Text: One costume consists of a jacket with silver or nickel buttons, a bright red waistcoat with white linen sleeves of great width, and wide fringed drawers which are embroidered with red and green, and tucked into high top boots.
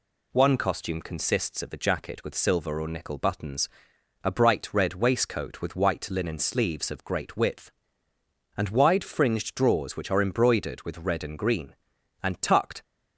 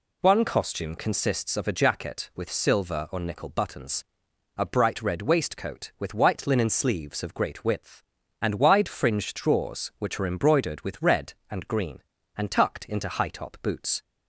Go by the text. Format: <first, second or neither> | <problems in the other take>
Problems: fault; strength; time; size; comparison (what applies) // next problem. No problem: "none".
second | stops before "into high top boots"; at 12.8 s